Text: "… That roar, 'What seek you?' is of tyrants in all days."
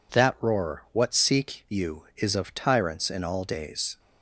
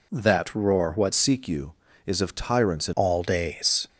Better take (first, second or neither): first